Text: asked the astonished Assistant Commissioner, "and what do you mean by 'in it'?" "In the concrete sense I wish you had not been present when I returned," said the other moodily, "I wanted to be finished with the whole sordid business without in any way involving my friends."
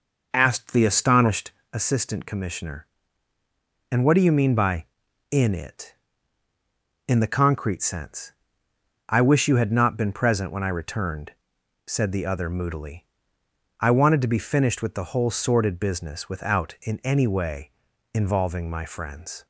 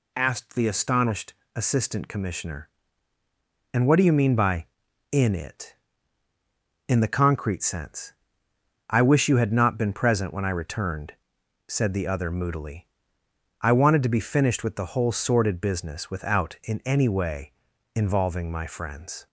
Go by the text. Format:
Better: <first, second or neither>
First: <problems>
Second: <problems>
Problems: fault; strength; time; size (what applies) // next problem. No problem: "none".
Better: second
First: starts louder than the rest; noticeable; until 1.8 s; 5.5 dB // pauses between "astonished" and "Assistant"; slight; at 1.5 s; 0.22 s long // pauses between "sense" and "I"; noticeable; at 8.3 s; 0.78 s long // pauses between "way" and "involving"; at 17.7 s; 0.42 s long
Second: pauses between "astonished" and "Assistant"; slight; at 1.3 s; 0.22 s long // pauses between "sense" and "I"; noticeable; at 8.1 s; 0.78 s long // pauses between "way" and "involving"; at 17.5 s; 0.42 s long